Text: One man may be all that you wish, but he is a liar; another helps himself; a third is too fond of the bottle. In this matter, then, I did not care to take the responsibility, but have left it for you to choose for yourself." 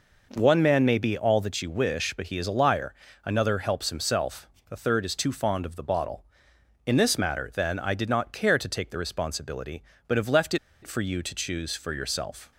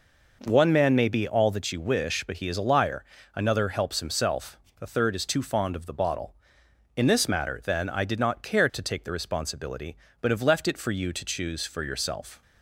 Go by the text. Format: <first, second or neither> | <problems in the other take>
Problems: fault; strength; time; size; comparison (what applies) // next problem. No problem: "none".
second | pauses between "left" and "it"; slight; at 10.5 s; 0.26 s long